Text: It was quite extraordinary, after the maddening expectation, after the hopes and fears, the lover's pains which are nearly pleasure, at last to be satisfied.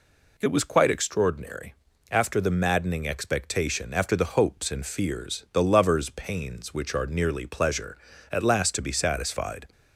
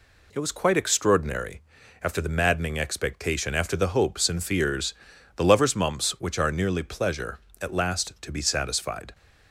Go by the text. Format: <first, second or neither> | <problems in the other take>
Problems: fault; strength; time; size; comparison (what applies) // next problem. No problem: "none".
first | says "mumps" for "pains"; at 5.7 s